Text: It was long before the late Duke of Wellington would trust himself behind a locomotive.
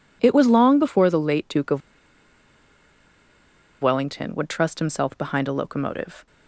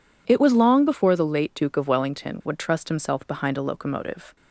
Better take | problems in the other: second | pauses between "of" and "Wellington"; strong; at 1.8 s; 2.0 s long

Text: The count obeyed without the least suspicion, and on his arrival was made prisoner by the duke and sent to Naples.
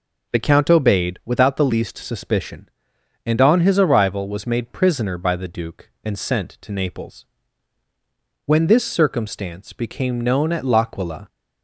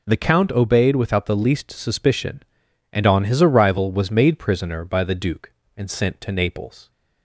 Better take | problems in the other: second | goes on to say "When this circumstance became known at L'Aquila"; strong; from 8.4 s on; 2.8 s long

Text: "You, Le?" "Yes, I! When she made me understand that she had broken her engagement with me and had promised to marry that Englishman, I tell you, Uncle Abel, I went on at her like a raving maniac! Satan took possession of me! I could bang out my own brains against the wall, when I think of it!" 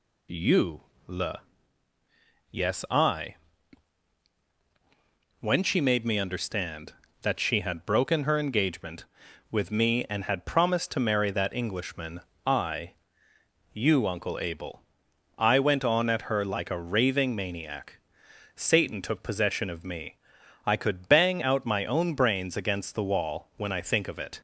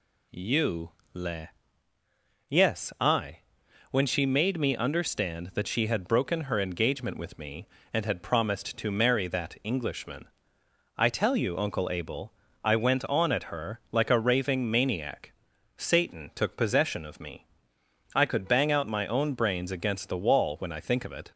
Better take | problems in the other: second | skips "tell"; at 13.3 s

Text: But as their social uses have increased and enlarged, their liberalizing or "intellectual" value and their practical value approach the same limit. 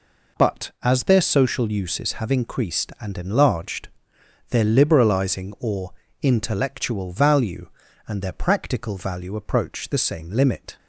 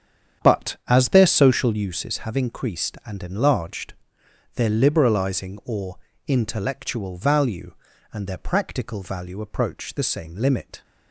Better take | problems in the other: first | starts louder than the rest; strong; until 1.9 s; 8.5 dB // pauses between "or" and "intellectual"; slight; at 5.9 s; 0.30 s long; slight in the first

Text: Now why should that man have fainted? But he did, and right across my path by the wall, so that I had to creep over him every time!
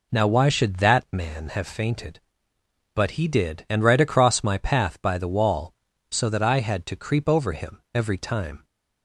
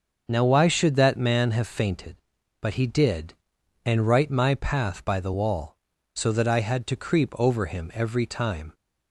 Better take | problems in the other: first | starts louder than the rest; until 1.3 s; 6.5 dB // skips "across"; at 4.3 s

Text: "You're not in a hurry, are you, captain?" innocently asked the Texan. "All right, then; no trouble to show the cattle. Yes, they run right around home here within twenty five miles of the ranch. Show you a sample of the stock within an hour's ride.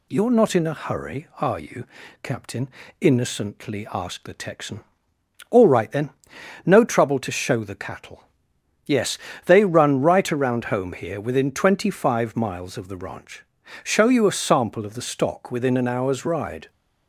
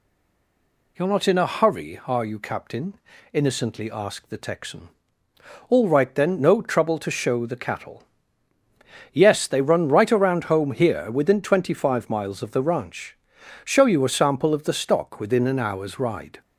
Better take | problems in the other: first | stays silent before the first word; slight; until 0.9 s; 0.9 s long

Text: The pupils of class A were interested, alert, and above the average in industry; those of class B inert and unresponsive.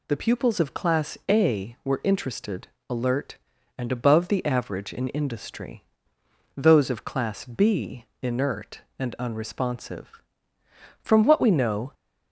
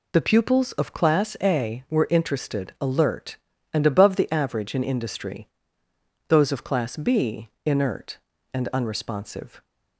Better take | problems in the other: second | pauses between "B" and "inert"; slight; at 8.0 s; 0.18 s long; slight in the second // goes on to say "From what we know"; noticeable; from 11.0 s on; 0.90 s long

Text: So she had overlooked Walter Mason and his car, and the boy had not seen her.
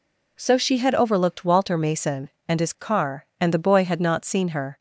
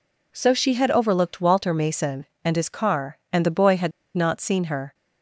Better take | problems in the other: first | pauses between "had" and "not"; slight; at 3.9 s; 0.24 s long

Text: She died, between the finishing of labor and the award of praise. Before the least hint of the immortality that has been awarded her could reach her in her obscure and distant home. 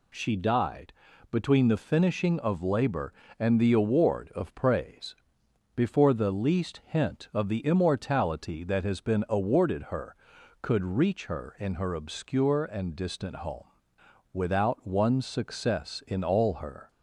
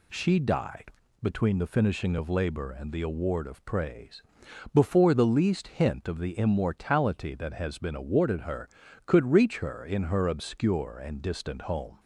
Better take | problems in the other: second | goes on to say "Without one success in all her"; strong; from 14.3 s on; 2.5 s long

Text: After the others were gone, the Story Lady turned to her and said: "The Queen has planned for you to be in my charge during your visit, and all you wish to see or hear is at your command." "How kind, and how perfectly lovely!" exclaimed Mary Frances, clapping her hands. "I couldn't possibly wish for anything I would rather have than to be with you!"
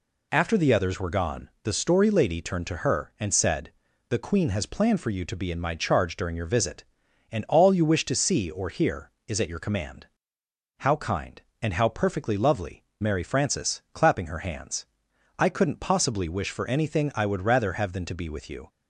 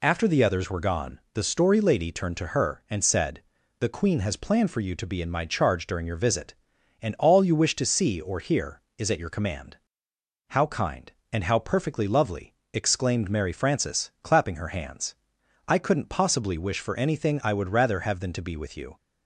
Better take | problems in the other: second | skips "exclaimed"; at 12.9 s

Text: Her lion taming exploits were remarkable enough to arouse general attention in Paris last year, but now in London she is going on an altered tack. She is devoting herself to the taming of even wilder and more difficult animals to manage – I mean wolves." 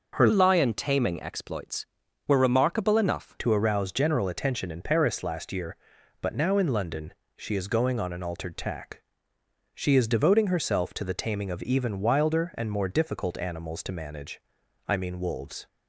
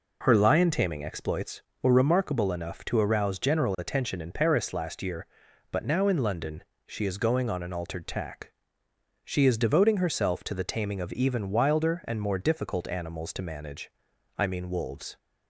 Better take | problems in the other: second | changes voice from "lion" to "enough"; from 0.3 to 3.3 s; 3.0 s long // pauses between "London" and "she"; slight; at 7.1 s; 0.24 s long; slight in the second

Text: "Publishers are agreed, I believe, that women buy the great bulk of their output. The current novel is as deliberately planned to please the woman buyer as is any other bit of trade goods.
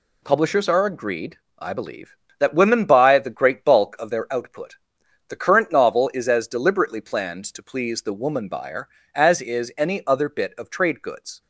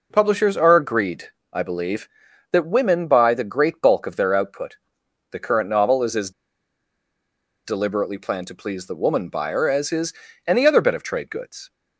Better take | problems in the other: first | pauses between "as" and "deliberately"; strong; at 6.3 s; 1.3 s long // pauses between "is" and "any"; slight; at 10.1 s; 0.34 s long

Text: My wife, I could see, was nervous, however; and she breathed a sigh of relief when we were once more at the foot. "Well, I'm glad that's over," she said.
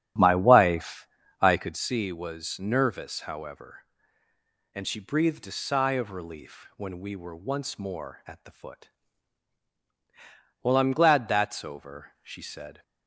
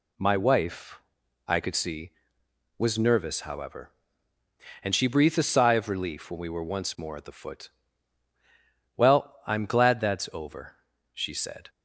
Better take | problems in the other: second | starts louder than the rest; strong; until 1.8 s; 9.5 dB

